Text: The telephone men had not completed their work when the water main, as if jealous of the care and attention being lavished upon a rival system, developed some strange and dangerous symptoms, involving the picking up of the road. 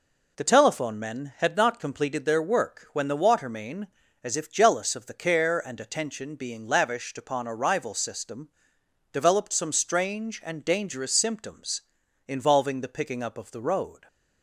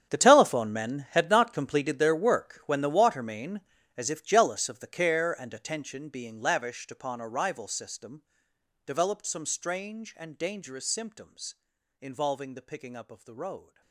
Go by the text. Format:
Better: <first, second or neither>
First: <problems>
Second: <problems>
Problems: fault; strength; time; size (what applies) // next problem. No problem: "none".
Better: first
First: none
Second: gets quieter; strong; throughout; 16.5 dB